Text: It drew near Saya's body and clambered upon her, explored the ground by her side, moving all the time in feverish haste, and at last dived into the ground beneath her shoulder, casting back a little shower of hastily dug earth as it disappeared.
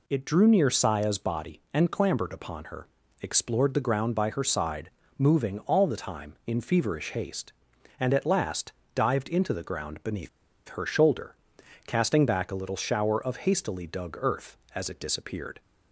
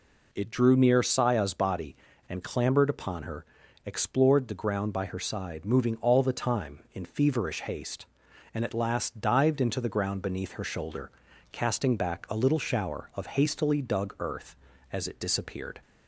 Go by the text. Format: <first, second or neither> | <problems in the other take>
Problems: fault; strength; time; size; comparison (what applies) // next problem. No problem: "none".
second | pauses between "last" and "dived"; slight; at 8.7 s; 0.24 s long // pauses between "beneath" and "her"; at 10.2 s; 0.41 s long